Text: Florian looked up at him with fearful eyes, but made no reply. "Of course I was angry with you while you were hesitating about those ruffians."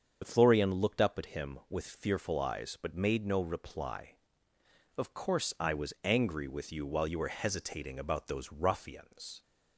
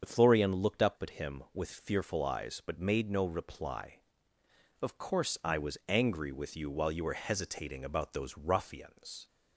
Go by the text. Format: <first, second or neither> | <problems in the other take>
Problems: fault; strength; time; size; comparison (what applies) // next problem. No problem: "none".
neither | starts louder than the rest; strong; the same in both